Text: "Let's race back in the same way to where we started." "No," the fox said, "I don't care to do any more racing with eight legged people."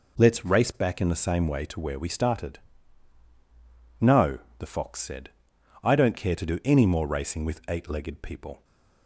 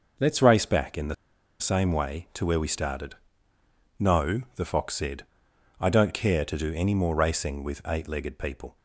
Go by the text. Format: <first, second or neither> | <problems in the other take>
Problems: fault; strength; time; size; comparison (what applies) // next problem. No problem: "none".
first | pauses between "the" and "same"; at 1.1 s; 0.45 s long